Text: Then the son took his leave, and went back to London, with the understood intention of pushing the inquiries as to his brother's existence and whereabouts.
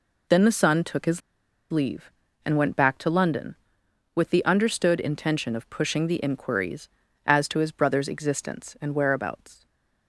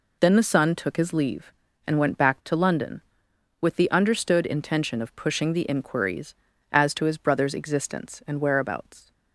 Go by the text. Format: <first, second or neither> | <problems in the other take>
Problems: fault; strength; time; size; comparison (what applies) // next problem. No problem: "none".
second | pauses between "his" and "leave"; noticeable; at 1.2 s; 0.50 s long // stays silent after the last word; slight; from 9.5 s on; 0.5 s long